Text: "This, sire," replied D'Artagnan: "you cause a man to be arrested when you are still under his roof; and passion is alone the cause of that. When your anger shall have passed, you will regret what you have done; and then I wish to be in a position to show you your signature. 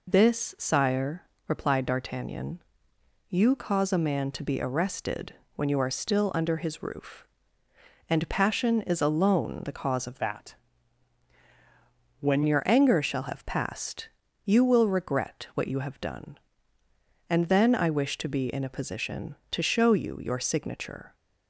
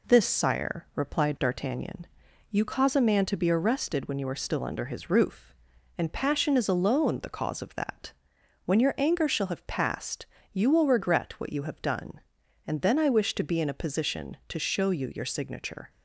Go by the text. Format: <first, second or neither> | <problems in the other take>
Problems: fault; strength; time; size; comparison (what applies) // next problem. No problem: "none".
second | pauses between "arrested" and "when"; slight; at 5.3 s; 0.20 s long // changes voice from "that" to "When"; from 10.1 to 12.4 s; 2.3 s long